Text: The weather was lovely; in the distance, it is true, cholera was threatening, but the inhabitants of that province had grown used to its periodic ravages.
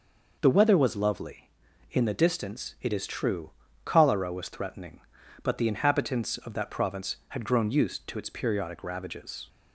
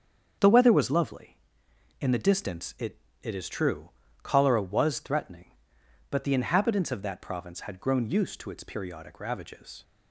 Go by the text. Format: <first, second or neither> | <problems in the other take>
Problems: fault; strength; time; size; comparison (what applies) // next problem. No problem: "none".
first | starts louder than the rest; strong; until 2.0 s; 7 dB // says "it" twice; at 3.2 s